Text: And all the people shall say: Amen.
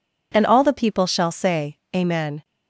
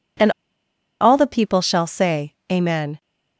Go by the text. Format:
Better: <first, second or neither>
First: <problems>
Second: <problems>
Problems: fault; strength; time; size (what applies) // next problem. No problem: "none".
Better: first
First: none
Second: pauses between "And" and "all"; noticeable; at 0.3 s; 0.68 s long